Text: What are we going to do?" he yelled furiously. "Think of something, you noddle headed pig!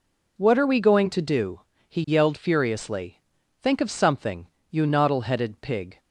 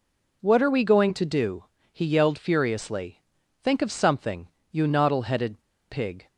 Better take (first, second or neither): first